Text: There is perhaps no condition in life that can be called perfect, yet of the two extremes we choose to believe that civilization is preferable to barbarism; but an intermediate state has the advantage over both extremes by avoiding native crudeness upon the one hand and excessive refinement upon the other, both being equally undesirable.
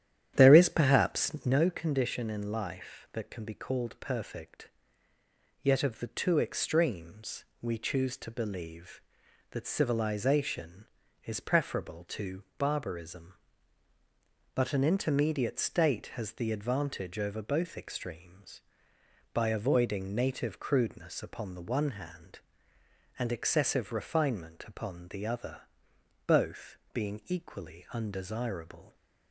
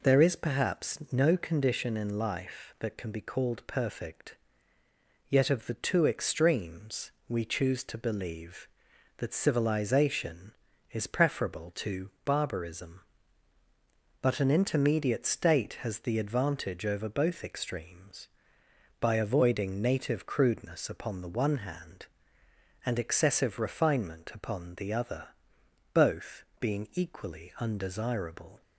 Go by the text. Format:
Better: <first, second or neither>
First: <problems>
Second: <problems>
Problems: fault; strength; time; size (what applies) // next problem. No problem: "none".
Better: second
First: starts louder than the rest; strong; until 1.6 s; 10.5 dB // pauses between "extremes" and "we"; slight; at 7.4 s; 0.18 s long // pauses between "both" and "being"; slight; at 26.7 s; 0.16 s long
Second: pauses between "extremes" and "we"; slight; at 7.1 s; 0.18 s long // pauses between "both" and "being"; slight; at 26.4 s; 0.16 s long